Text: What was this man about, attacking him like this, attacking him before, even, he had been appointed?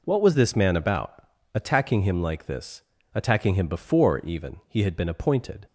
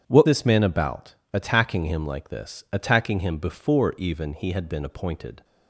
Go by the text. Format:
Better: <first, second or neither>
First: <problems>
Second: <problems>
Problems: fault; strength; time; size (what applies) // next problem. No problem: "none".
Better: first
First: none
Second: starts louder than the rest; strong; until 1.0 s; 8.5 dB // skips "was"; at 0.2 s